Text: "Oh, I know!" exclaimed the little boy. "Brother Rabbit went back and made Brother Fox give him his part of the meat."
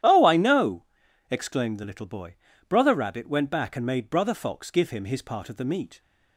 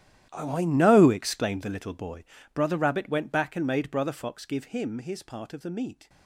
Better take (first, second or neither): first